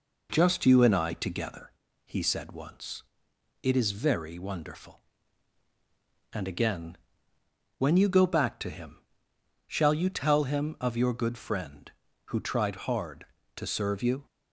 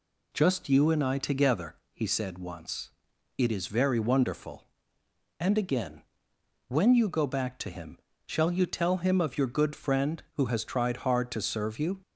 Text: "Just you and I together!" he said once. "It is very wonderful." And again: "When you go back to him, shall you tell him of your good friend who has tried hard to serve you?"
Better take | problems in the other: second | skips "has"; at 12.3 s

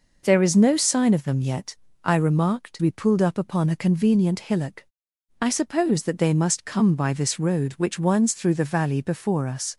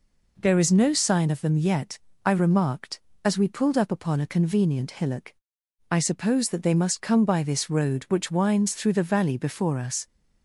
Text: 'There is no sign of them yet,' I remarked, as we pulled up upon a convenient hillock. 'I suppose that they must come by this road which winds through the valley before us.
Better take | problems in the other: second | skips "as"; at 2.7 s

